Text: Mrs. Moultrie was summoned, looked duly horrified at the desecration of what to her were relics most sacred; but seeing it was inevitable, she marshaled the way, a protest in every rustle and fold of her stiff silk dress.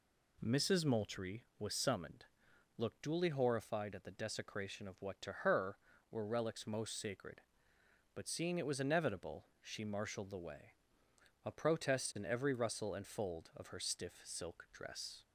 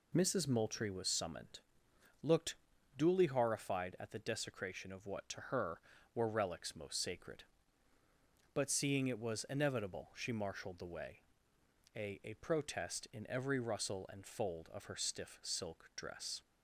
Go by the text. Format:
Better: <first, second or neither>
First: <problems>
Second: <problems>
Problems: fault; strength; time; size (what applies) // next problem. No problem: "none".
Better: first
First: none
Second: pauses between "looked" and "duly"; at 2.5 s; 0.42 s long // says "a" twice; at 12.2 s